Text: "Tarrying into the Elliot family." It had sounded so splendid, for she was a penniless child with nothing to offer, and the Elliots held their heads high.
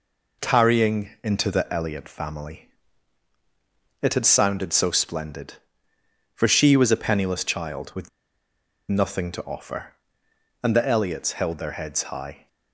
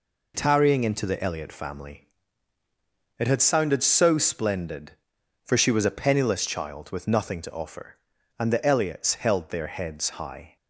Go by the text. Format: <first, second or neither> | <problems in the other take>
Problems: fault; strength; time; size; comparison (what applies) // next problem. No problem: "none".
second | pauses between "with" and "nothing"; noticeable; at 8.0 s; 0.80 s long